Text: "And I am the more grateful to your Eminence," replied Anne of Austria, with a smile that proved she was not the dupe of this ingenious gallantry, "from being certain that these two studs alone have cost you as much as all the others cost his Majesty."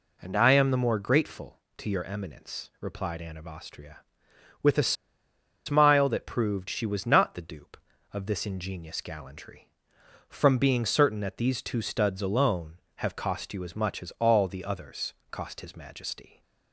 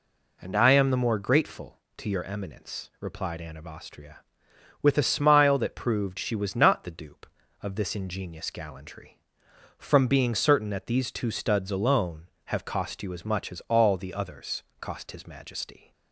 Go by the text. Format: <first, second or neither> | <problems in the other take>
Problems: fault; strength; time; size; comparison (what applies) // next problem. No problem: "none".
second | pauses between "a" and "smile"; noticeable; at 4.9 s; 0.73 s long // pauses between "others" and "cost"; slight; at 15.1 s; 0.16 s long; slight in the second